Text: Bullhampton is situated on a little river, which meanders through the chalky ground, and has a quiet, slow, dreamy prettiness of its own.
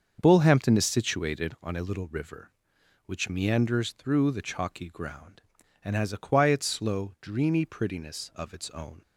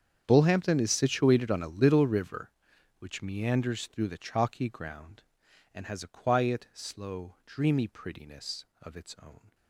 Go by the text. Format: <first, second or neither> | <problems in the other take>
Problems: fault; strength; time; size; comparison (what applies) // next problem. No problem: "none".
first | gets quieter; strong; throughout; 20 dB // starts louder than the rest; strong; until 1.2 s; 7.5 dB; also in the first